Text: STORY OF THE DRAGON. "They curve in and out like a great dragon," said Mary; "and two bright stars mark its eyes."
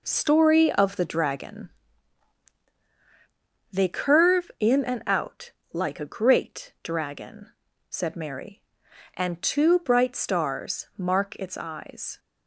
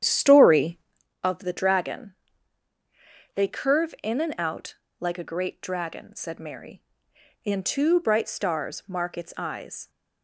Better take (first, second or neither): first